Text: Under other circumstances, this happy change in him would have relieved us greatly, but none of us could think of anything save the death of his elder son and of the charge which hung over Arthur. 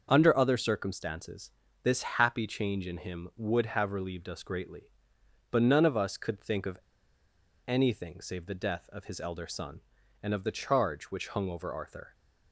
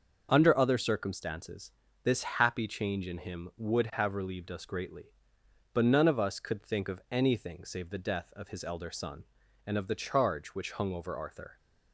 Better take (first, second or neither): second